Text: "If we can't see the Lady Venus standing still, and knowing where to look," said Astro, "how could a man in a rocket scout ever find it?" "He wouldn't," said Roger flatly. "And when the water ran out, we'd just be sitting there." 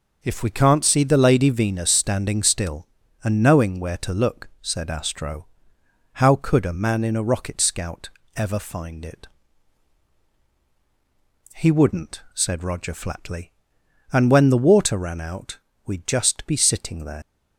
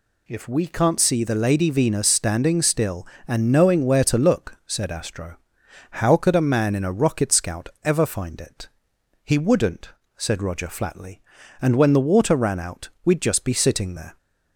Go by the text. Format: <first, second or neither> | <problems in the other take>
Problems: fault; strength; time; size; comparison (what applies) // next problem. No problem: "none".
second | pauses between "scout" and "ever"; slight; at 8.0 s; 0.26 s long; slight in the second // leaves "there" unfinished; at 17.2 s; 145 ms